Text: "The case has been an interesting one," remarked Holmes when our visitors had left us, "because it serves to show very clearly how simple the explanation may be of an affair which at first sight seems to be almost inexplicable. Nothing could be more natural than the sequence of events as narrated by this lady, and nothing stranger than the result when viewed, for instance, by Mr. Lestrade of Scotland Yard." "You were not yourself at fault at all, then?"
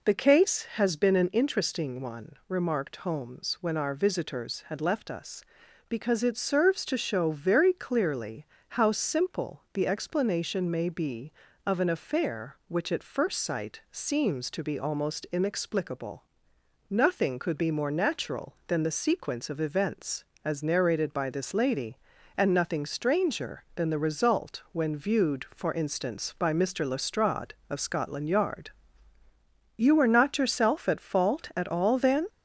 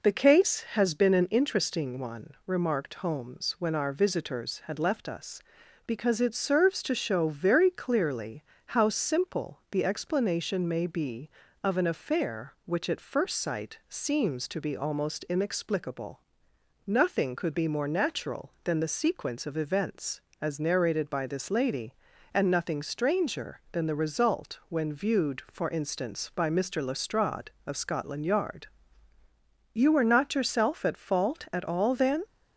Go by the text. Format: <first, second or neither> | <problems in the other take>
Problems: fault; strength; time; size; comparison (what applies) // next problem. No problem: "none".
second | gets louder; slight; throughout; 2 dB // pauses between "clearly" and "how"; slight; at 8.4 s; 0.24 s long; slight in the second